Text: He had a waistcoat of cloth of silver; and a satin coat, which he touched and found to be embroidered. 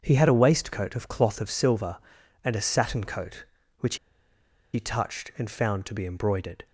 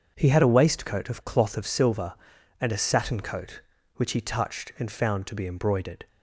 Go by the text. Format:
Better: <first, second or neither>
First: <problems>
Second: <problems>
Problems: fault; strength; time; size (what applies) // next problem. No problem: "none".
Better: second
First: starts louder than the rest; until 1.0 s; 6.5 dB // pauses between "which" and "he"; noticeable; at 3.9 s; 0.77 s long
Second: starts louder than the rest; until 1.1 s; 6.5 dB